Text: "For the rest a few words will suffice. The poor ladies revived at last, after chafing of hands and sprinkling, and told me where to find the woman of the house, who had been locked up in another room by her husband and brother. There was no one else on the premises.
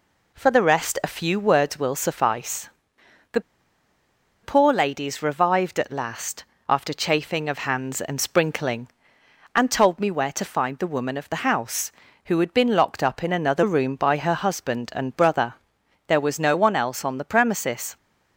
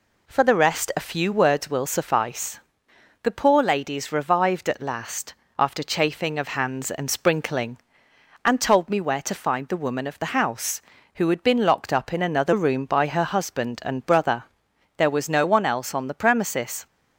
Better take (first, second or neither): second